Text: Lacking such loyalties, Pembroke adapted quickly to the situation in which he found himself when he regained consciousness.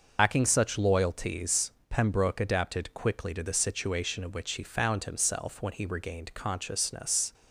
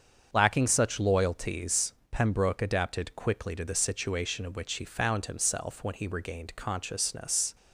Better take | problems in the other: second | loses the start of "Lacking"; at 0.1 s; 80 ms // starts louder than the rest; noticeable; until 1.2 s; 6 dB; also in the second

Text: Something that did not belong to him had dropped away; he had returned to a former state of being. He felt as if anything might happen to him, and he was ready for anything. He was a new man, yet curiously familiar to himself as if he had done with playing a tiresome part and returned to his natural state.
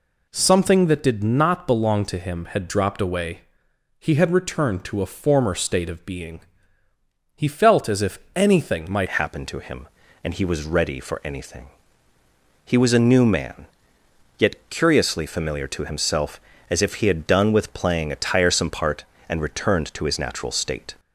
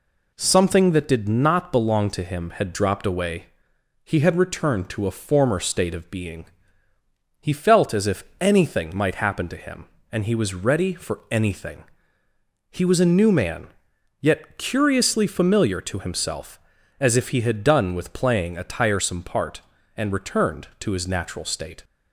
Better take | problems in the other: second | pauses between "if" and "anything"; slight; at 8.1 s; 0.18 s long; slight in the second // changes voice at "happen"; from 9.0 s on; 11.9 s long

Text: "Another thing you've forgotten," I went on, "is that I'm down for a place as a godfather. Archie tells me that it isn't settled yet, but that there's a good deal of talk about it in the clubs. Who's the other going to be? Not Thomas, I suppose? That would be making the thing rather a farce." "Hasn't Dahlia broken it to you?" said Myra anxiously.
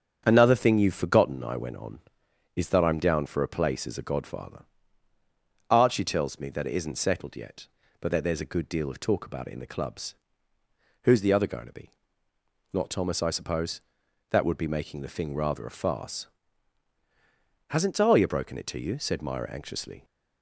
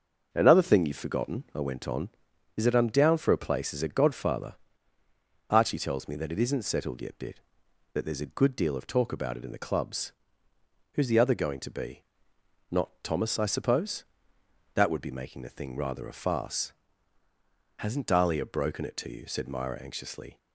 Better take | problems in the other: first | starts louder than the rest; until 1.3 s; 6.5 dB; strong in the first // says "bit" for "but"; at 7.1 s

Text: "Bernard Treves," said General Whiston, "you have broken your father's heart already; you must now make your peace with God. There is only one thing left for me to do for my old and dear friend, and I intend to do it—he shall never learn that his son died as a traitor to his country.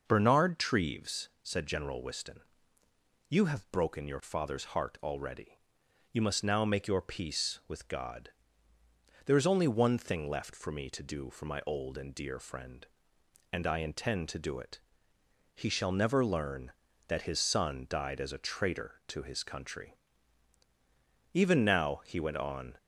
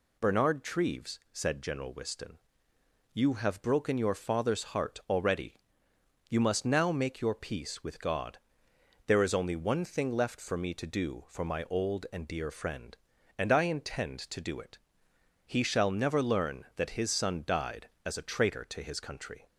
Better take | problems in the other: second | goes on to say "Even now he went on"; from 21.3 s on; 1.4 s long

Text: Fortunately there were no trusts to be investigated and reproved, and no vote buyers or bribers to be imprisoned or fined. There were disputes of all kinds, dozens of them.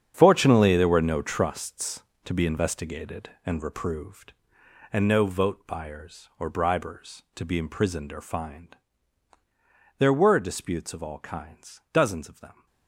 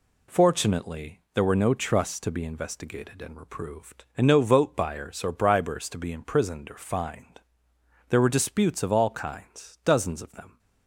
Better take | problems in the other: second | gets quieter; strong; throughout; 13 dB

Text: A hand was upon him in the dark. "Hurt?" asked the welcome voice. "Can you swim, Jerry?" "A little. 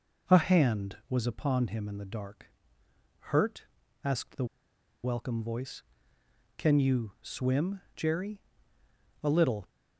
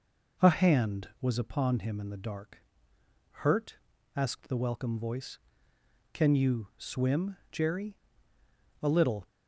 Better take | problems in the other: second | pauses between "the" and "welcome"; noticeable; at 4.4 s; 0.58 s long

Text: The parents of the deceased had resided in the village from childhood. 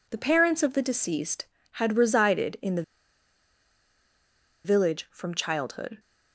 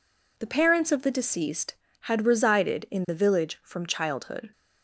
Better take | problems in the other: second | pauses between "the" and "village"; strong; at 2.8 s; 1.8 s long

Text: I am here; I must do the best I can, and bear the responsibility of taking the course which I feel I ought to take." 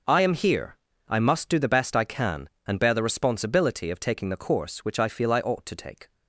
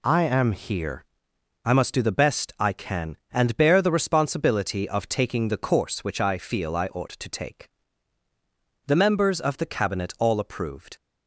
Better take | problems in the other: first | goes on to say "The members of the cabinet all approved"; strong; from 8.8 s on; 2.1 s long

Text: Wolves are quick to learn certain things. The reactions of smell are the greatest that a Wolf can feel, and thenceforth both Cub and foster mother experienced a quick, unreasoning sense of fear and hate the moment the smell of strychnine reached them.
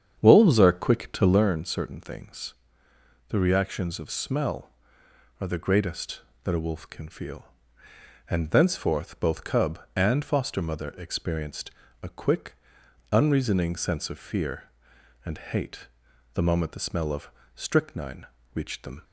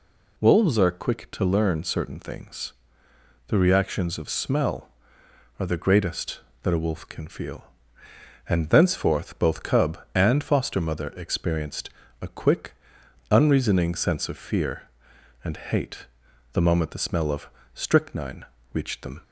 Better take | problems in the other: second | starts louder than the rest; strong; until 1.5 s; 8 dB // pauses between "experienced" and "a"; slight; at 11.6 s; 0.32 s long; slight in the second // pauses between "hate" and "the"; noticeable; at 15.8 s; 0.48 s long; noticeable in the second // pauses between "of" and "strychnine"; slight; at 17.2 s; 0.24 s long; slight in the second // pauses between "strychnine" and "reached"; slight; at 18.2 s; 0.30 s long; slight in the second

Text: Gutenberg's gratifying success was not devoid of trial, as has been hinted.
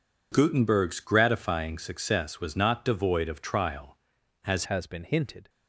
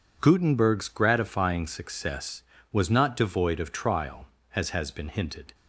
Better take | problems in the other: second | changes voice at "has"; from 4.6 s on; 0.8 s long

